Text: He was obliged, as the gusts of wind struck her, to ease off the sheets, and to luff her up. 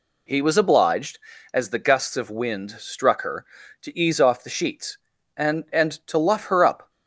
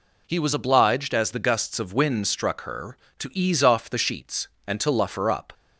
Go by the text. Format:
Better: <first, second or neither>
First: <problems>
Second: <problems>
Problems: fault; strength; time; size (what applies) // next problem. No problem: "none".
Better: second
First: says "and" twice; at 5.7 s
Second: none